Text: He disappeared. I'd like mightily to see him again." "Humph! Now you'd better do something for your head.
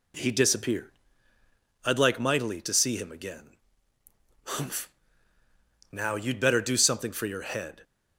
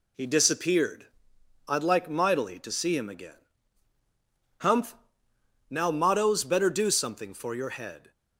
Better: first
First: none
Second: says "mottos" for "you'd"; at 5.9 s

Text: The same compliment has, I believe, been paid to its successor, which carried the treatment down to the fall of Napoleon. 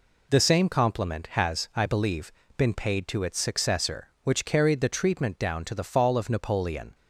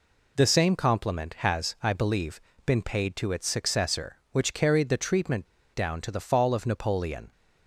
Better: first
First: none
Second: pauses between "treatment" and "down"; slight; at 5.4 s; 0.28 s long

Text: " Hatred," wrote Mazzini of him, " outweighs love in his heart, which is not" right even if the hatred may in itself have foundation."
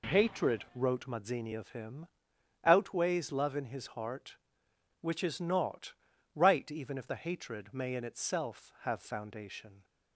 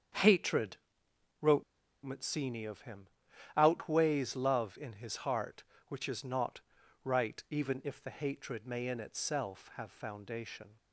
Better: first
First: pauses between "not" and "right"; at 5.9 s; 0.42 s long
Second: starts louder than the rest; until 2.1 s; 7 dB // pauses between "wrote" and "Mazzini"; at 1.6 s; 0.39 s long // pauses between "not" and "right"; at 6.6 s; 0.42 s long

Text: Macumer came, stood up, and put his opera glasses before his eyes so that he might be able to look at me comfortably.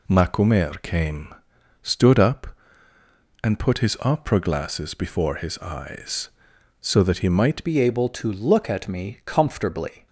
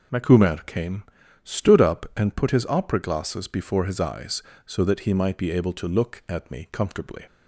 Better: second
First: changes voice at "be"; from 7.6 s on; 2.4 s long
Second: none

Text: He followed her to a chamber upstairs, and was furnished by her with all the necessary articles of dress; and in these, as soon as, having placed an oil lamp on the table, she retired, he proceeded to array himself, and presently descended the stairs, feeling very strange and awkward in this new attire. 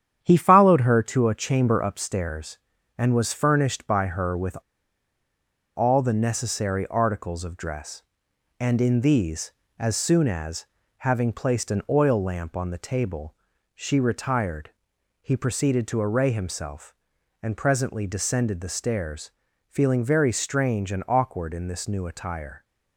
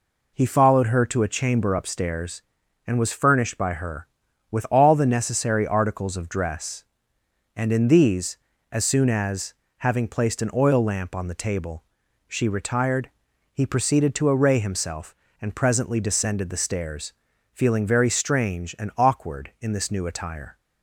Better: second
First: starts louder than the rest; strong; until 1.2 s; 9.5 dB // pauses between "with" and "all"; at 4.5 s; 1.1 s long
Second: none

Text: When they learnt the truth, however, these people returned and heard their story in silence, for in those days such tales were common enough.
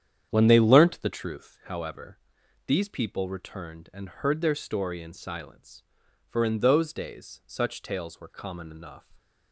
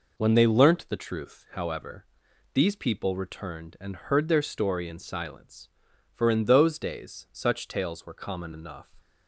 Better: second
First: starts louder than the rest; strong; until 1.3 s; 9 dB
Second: none

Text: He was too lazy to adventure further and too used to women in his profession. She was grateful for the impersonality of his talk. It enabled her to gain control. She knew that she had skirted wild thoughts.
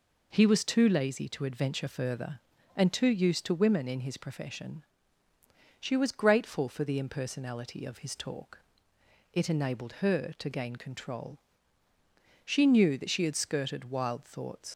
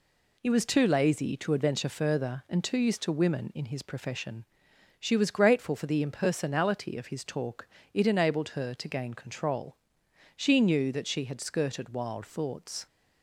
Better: second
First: leaves "thoughts" unfinished; at 14.7 s; 115 ms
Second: none

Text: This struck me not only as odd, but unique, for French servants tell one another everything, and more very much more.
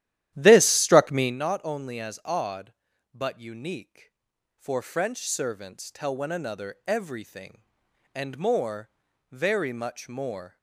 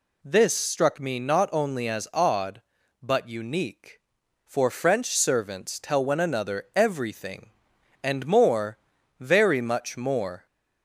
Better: second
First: starts louder than the rest; strong; until 1.4 s; 12.5 dB // pauses between "more" and "very"; at 8.8 s; 0.40 s long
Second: pauses between "more" and "very"; at 8.7 s; 0.40 s long

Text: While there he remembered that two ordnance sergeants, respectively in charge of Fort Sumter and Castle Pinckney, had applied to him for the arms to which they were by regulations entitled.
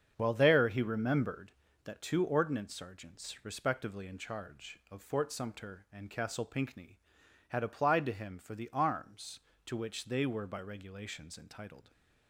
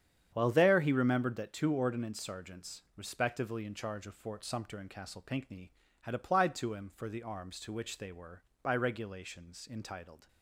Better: neither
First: starts louder than the rest; strong; until 1.1 s; 7.5 dB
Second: starts louder than the rest; strong; until 1.3 s; 8.5 dB

